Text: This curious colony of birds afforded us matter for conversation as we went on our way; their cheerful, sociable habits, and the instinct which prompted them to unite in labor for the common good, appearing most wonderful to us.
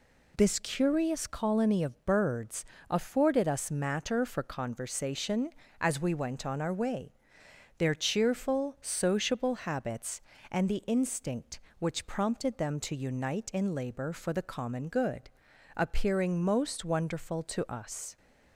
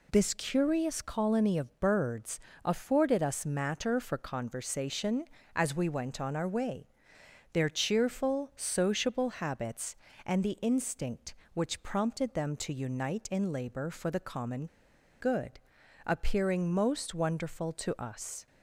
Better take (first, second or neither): first